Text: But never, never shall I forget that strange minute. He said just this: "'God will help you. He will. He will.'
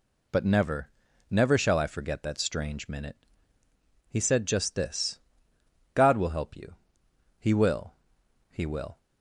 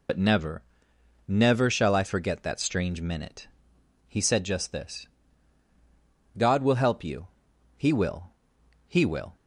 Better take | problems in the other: first | loses the start of "But"; at 0.0 s; 65 ms

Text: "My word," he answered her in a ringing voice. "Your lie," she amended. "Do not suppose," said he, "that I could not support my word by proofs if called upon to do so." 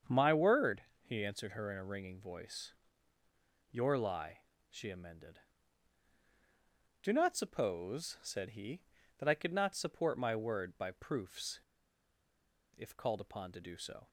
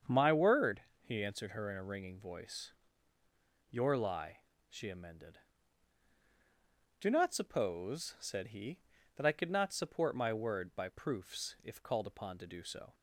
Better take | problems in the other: second | starts louder than the rest; strong; until 1.2 s; 7 dB; strong in the second // pauses between "proofs" and "if"; at 11.6 s; 1.1 s long

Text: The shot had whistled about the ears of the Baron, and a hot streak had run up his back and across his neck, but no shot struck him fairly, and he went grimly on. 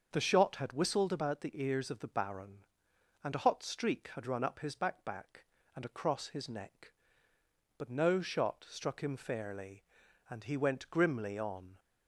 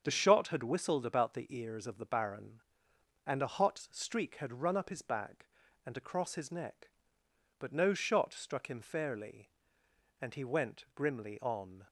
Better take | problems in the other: second | starts louder than the rest; until 1.1 s; 6.5 dB; strong in the second // says "back" twice; at 5.0 s

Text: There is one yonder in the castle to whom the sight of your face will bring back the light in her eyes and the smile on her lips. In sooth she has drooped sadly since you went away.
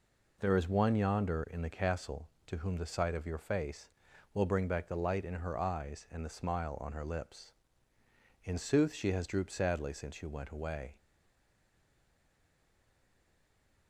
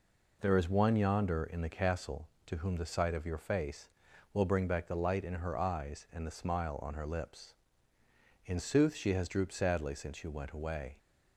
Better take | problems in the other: second | stays silent after the last word; strong; from 10.9 s on; 2.9 s long

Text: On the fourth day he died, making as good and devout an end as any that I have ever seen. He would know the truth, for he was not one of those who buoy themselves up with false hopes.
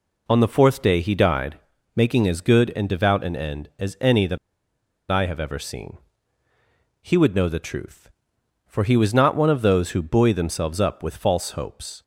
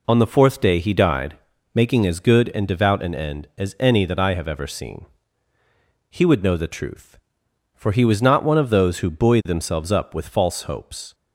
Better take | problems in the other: second | pauses between "that" and "I"; noticeable; at 4.3 s; 0.72 s long

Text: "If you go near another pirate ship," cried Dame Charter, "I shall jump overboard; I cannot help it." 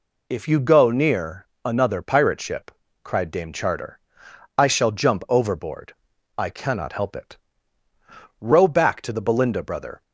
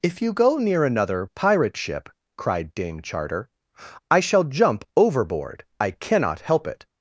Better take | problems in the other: second | pauses between "near" and "another"; slight; at 1.4 s; 0.18 s long // goes on to say "Row back to the Belinda brother"; from 8.3 s on; 1.6 s long

